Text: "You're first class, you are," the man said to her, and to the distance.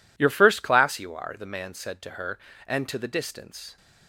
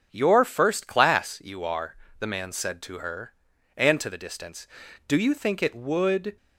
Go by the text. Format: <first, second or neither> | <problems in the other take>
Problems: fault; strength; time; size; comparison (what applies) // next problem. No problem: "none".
first | starts louder than the rest; until 1.1 s; 7 dB // goes on to say "Do you think it would"; noticeable; from 5.0 s on; 1.3 s long